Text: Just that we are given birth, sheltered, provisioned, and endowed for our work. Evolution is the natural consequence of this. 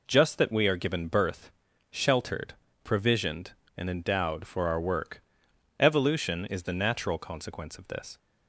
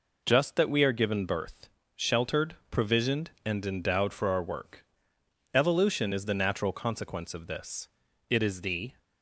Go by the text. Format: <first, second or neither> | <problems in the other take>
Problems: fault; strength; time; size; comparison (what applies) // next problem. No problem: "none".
first | goes on to say "It is the"; noticeable; from 8.2 s on; 0.72 s long